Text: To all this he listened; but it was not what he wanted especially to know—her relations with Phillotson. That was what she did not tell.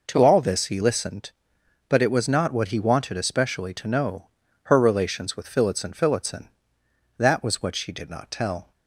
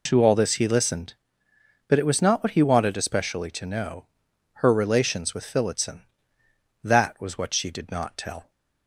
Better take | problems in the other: second | says "Phillotson" twice; at 5.9 s

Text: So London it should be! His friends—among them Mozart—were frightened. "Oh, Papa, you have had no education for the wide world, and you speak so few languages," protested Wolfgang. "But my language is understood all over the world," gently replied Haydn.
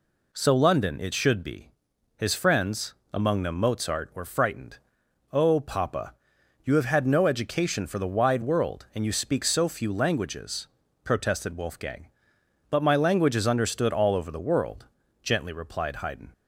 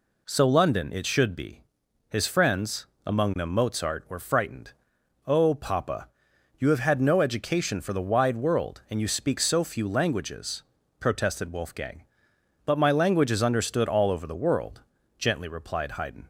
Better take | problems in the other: neither | none

